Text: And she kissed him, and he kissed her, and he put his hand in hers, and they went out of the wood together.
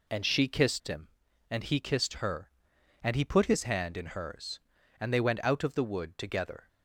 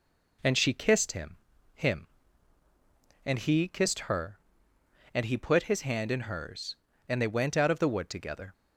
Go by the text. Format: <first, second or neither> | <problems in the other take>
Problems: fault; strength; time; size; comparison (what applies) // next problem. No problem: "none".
first | says "him" twice; at 1.7 s